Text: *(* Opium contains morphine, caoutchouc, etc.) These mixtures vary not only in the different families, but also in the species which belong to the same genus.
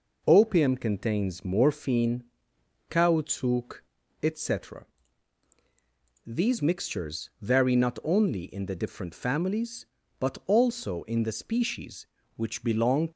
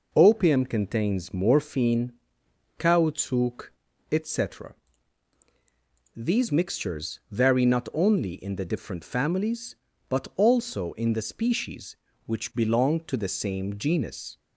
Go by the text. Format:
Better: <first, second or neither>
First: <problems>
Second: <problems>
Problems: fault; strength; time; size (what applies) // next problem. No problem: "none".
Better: second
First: stops before "to the same genus"; at 13.1 s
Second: none